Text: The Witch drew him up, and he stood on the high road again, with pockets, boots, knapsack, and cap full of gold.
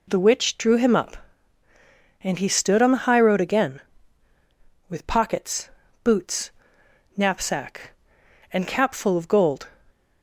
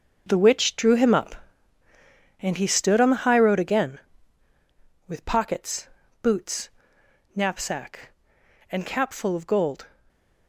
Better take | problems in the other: first | gets quieter; strong; throughout; 11.5 dB // stays silent after the last word; slight; from 9.8 s on; 0.6 s long

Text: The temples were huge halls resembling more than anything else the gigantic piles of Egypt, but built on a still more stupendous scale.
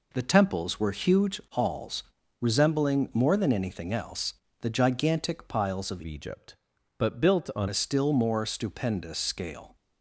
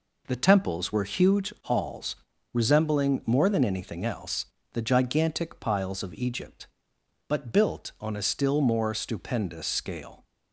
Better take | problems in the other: second | pauses between "halls" and "resembling"; at 2.0 s; 0.38 s long; also in the second // pauses between "else" and "the"; slight; at 4.3 s; 0.28 s long; slight in the second // changes voice from "Egypt" to "on"; from 6.0 to 7.6 s; 1.6 s long

